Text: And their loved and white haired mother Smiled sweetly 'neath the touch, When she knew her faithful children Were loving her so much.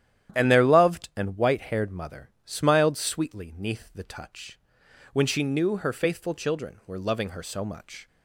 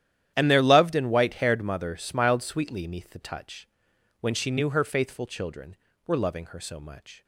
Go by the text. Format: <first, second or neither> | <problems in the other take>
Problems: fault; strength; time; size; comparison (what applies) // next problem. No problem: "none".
neither | starts louder than the rest; strong; the same in both